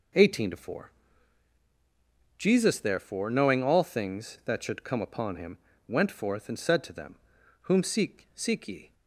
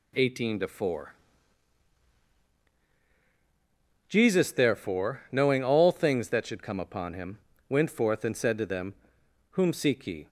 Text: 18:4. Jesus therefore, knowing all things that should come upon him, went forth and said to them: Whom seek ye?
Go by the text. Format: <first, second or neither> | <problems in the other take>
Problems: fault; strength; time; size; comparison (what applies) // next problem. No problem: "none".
second | says "seek" twice; at 8.3 s